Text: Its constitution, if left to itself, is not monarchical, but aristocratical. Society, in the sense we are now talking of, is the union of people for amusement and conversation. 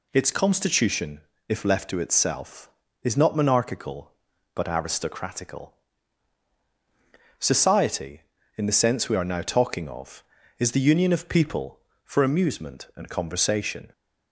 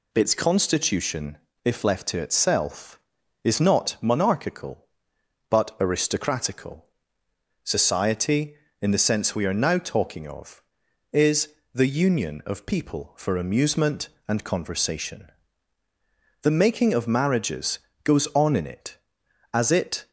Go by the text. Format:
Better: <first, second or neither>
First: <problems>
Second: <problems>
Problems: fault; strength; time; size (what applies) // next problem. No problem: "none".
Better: first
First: none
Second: pauses between "is" and "the"; slight; at 11.5 s; 0.22 s long // goes on to say "The making of marriages goes on in it as it"; strong; from 16.4 s on; 3.6 s long